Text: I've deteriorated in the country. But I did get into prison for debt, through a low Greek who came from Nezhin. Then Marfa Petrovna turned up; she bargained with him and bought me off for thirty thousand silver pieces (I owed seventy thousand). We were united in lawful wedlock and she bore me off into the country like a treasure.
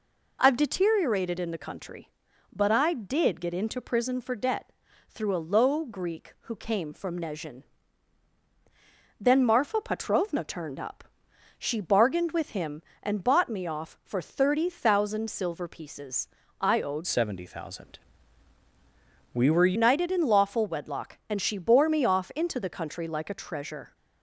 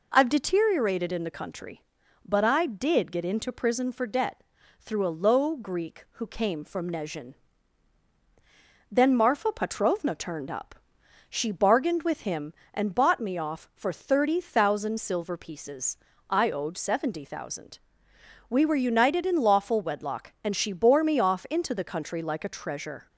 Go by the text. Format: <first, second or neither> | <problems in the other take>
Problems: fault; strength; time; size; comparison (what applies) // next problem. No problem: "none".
second | changes voice from "seventy" to "were"; from 17.0 to 19.7 s; 2.7 s long